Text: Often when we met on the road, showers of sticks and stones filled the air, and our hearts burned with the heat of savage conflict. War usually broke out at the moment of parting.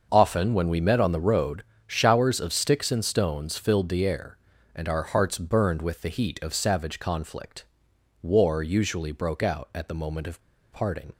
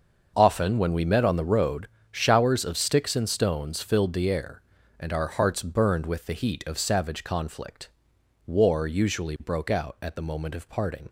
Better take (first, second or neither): second